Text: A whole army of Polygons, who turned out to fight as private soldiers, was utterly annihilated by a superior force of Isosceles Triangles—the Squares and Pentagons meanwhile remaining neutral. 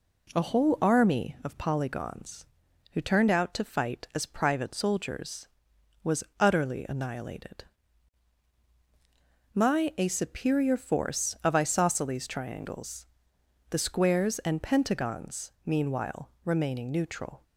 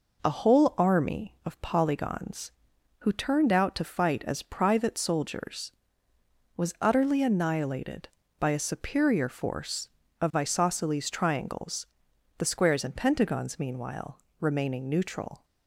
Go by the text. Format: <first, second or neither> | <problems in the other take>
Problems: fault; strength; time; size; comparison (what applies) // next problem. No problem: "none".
second | pauses between "was" and "utterly"; slight; at 6.2 s; 0.16 s long // says "my" for "by"; at 9.5 s // pauses between "meanwhile" and "remaining"; slight; at 16.2 s; 0.16 s long; slight in the second